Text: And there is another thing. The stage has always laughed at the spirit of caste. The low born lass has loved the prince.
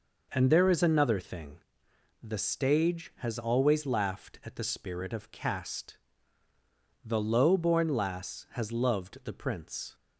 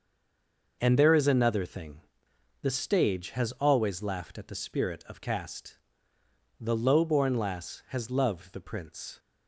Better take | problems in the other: first | stays silent before the first word; slight; until 0.8 s; 0.8 s long // starts louder than the rest; noticeable; until 1.8 s; 6 dB

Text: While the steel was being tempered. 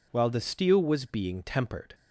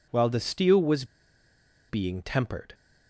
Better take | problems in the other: first | pauses between "was" and "being"; noticeable; at 1.0 s; 0.85 s long

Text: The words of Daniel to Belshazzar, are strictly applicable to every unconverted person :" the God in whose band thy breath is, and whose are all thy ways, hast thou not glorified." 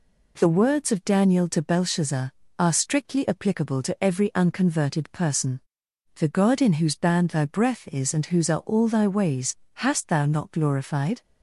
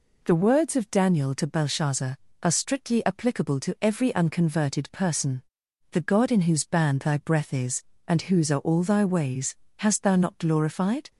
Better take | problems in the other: neither | none

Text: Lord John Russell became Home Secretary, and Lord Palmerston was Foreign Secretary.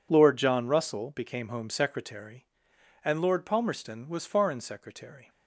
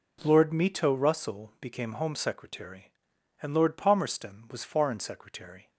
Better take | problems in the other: first | says "Mito" for "John"; at 0.5 s

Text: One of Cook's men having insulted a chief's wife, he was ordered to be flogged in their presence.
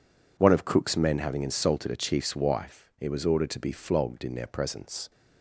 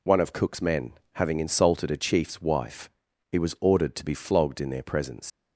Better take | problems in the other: first | pauses between "men" and "having"; slight; at 0.9 s; 0.22 s long // leaves "presence" unfinished; at 5.2 s; 110 ms

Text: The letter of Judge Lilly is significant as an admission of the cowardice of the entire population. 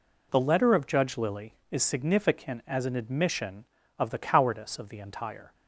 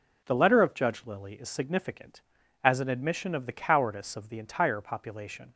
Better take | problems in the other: second | stops before "population"; at 5.5 s

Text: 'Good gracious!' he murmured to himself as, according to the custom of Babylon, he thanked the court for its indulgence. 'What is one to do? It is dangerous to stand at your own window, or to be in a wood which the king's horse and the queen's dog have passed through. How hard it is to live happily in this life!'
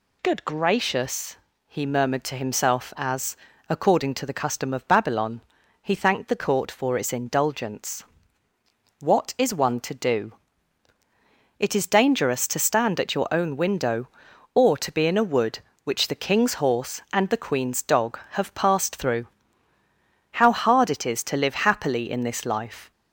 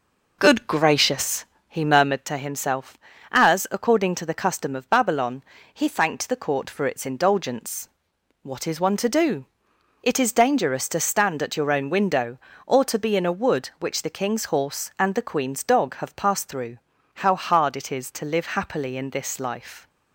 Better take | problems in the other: first | starts louder than the rest; noticeable; until 2.3 s; 5 dB

